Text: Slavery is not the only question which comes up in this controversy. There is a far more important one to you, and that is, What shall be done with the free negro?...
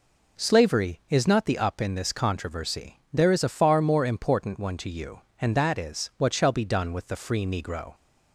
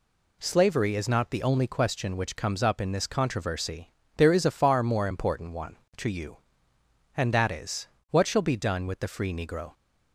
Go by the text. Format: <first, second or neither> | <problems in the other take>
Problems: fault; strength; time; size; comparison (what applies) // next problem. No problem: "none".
second | skips "only question which comes"; at 1.5 s